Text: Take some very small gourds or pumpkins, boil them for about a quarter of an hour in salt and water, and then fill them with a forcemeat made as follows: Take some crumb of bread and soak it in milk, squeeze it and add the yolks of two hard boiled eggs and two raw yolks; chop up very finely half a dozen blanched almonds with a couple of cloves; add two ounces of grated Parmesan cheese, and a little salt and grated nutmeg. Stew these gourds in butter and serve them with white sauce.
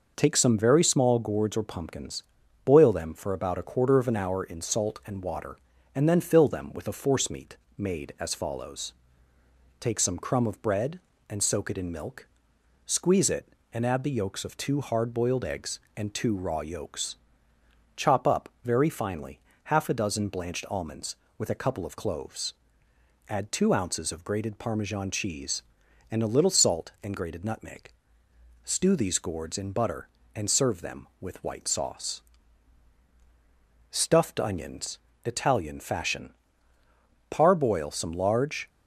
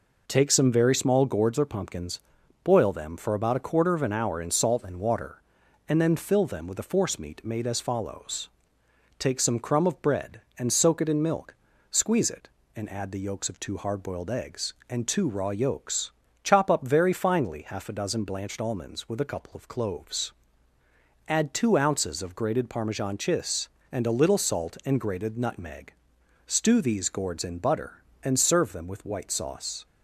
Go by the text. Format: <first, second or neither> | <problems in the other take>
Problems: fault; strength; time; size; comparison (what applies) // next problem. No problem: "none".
second | pauses between "forcemeat" and "made"; slight; at 7.5 s; 0.20 s long // pauses between "up" and "very"; slight; at 18.4 s; 0.16 s long // pauses between "finely" and "half"; slight; at 19.3 s; 0.26 s long // goes on to say "STUFFED ONIONS ITALIAN FASHION Parboil some large"; strong; from 33.9 s on; 4.7 s long